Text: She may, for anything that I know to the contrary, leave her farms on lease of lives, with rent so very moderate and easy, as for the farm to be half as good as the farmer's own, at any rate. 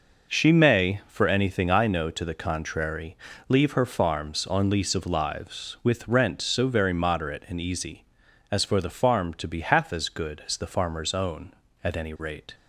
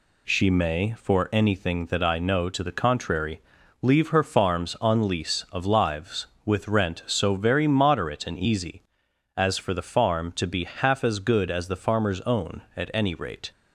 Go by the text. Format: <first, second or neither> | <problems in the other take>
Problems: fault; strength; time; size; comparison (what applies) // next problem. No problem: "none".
second | skips "that"; at 1.7 s